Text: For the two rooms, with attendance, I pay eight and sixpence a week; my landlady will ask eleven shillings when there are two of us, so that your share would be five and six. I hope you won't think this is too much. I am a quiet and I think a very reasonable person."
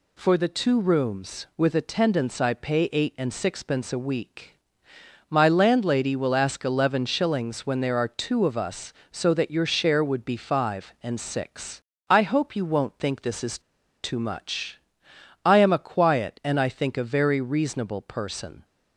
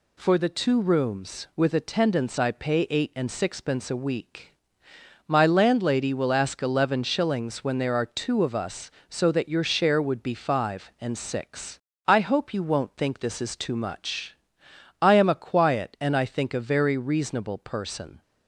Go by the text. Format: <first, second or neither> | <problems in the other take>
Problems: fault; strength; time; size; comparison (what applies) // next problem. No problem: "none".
second | pauses between "is" and "too"; at 13.5 s; 0.44 s long